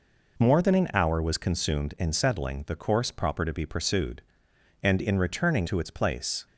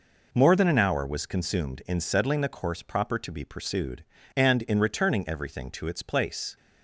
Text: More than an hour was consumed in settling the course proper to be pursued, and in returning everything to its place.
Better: second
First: skips "everything"; at 5.6 s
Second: none

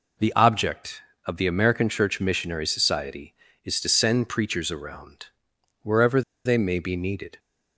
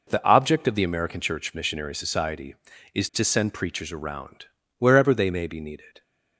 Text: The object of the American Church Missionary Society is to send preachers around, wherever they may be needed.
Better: second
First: pauses between "wherever" and "they"; slight; at 6.2 s; 0.24 s long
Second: none

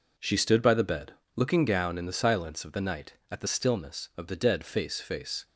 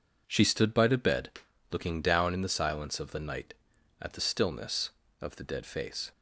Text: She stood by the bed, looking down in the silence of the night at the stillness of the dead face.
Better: second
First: says "face" twice; at 5.0 s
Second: none

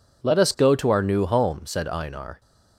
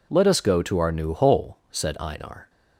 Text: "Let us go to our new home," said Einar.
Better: first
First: none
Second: says "hole" for "home"; at 1.1 s

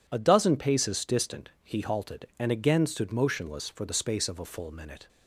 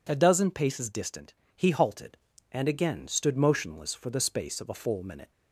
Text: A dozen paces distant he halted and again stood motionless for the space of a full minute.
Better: neither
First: pauses between "distant" and "he"; slight; at 1.4 s; 0.16 s long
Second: pauses between "distant" and "he"; slight; at 1.3 s; 0.22 s long

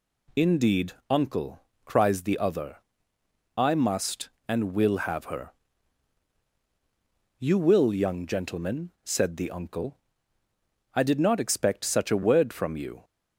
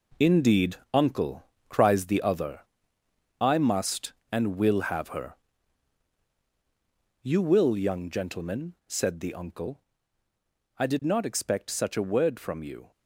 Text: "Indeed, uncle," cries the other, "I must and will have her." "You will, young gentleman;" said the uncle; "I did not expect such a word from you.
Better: first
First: none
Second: gets quieter; strong; throughout; 9 dB

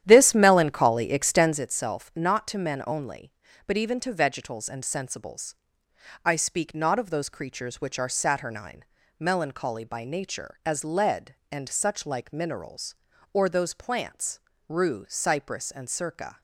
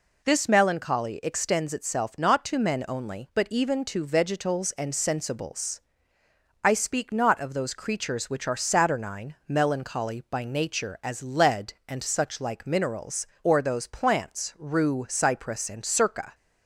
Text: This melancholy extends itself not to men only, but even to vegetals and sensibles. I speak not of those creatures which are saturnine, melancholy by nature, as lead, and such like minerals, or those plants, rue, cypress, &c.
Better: second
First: starts louder than the rest; strong; until 1.6 s; 10.5 dB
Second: none

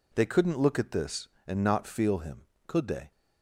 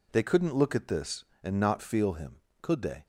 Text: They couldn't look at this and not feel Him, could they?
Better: neither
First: none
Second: none

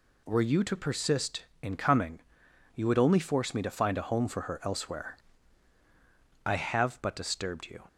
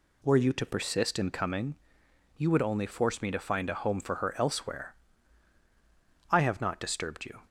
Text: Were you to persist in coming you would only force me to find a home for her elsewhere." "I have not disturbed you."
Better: second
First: pauses between "coming" and "you"; noticeable; at 2.1 s; 0.54 s long // says "but" for "not"; at 7.0 s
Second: pauses between "coming" and "you"; noticeable; at 1.7 s; 0.62 s long

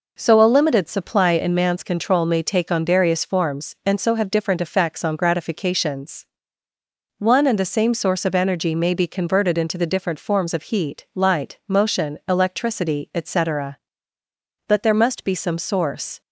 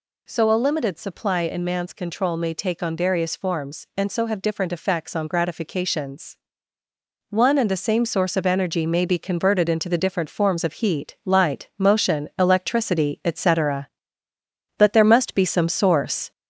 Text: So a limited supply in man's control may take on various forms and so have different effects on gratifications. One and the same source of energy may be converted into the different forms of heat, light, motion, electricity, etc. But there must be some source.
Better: first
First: none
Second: gets louder; throughout; 4 dB

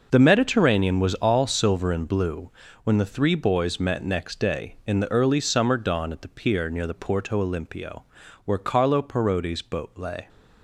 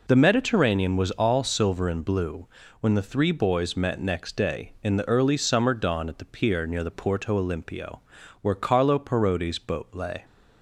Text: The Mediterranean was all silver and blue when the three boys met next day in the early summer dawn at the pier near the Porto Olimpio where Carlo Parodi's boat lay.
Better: second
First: gets quieter; strong; throughout; 11 dB // pauses between "blue" and "when"; slight; at 2.5 s; 0.34 s long // pauses between "Olimpio" and "where"; at 8.0 s; 0.40 s long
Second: pauses between "blue" and "when"; slight; at 2.4 s; 0.34 s long // pauses between "Olimpio" and "where"; at 8.0 s; 0.40 s long

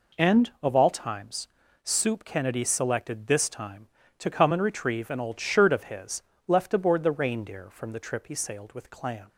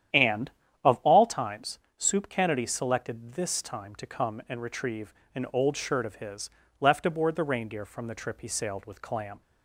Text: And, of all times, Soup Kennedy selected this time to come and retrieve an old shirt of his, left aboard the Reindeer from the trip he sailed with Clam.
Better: first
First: none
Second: starts louder than the rest; strong; until 1.2 s; 10 dB // pauses between "retrieve" and "an"; slight; at 5.1 s; 0.22 s long

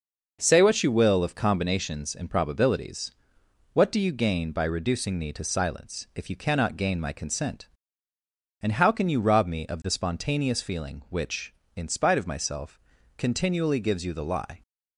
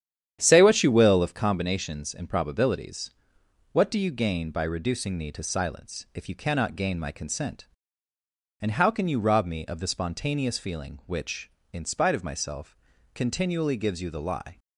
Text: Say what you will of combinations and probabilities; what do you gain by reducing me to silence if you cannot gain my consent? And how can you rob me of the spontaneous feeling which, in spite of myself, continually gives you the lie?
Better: first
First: none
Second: starts louder than the rest; strong; until 1.4 s; 9.5 dB

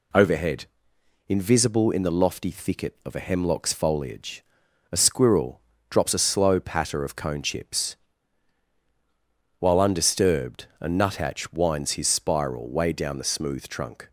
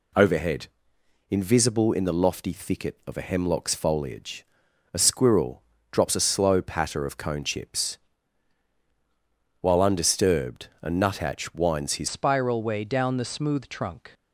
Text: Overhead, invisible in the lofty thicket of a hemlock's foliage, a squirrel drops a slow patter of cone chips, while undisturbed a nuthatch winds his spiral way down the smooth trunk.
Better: first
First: pauses between "squirrel" and "drops"; slight; at 5.6 s; 0.28 s long // pauses between "undisturbed" and "a"; slight; at 10.6 s; 0.16 s long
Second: pauses between "squirrel" and "drops"; slight; at 5.6 s; 0.28 s long // pauses between "undisturbed" and "a"; slight; at 10.6 s; 0.16 s long // changes voice at "spiral"; from 12.0 s on; 2.1 s long

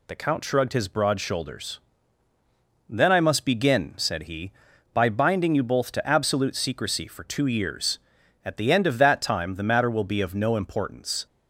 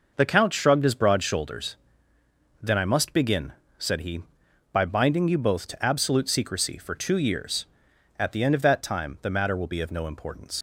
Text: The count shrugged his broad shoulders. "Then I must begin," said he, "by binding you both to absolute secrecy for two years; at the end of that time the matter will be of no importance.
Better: first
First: none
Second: starts louder than the rest; noticeable; until 1.1 s; 6 dB // leaves "importance" unfinished; at 10.5 s; 125 ms

